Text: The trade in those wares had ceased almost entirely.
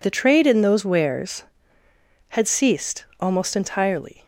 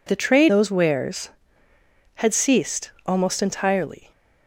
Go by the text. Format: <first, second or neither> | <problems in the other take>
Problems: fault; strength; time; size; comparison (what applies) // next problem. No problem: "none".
first | skips "in"; at 0.4 s